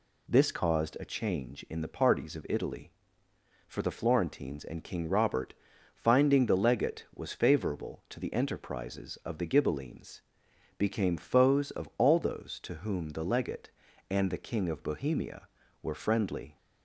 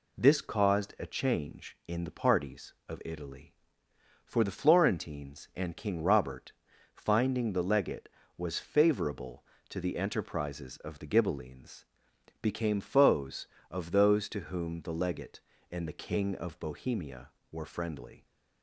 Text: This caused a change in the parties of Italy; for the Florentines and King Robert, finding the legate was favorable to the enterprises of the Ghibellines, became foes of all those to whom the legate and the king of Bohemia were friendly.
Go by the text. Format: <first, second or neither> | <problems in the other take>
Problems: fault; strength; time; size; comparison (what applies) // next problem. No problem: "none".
first | skips "all"; at 13.9 s